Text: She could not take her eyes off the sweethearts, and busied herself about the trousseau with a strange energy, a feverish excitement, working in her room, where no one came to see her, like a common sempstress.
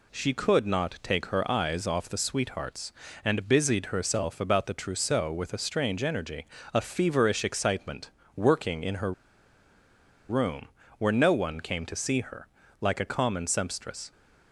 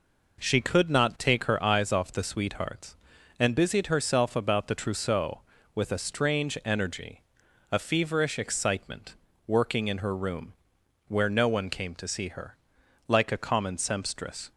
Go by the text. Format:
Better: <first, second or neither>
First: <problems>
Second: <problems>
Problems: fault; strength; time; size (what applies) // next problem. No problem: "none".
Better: second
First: pauses between "her" and "room"; at 9.1 s; 1.1 s long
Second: none